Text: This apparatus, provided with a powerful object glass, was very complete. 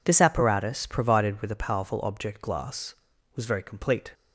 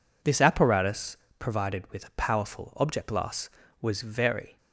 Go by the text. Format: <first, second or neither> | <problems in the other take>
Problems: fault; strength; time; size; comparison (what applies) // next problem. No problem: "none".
first | stops before "complete"; at 4.5 s